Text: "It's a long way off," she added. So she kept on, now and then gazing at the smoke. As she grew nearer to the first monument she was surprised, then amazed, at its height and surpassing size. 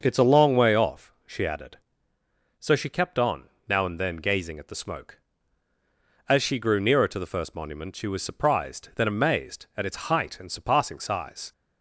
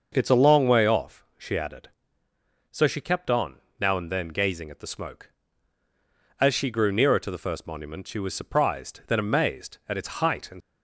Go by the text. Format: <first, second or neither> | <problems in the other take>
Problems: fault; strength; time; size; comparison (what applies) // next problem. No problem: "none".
first | starts louder than the rest; until 1.1 s; 6 dB; also in the first // stops before "surpassing size"; at 10.6 s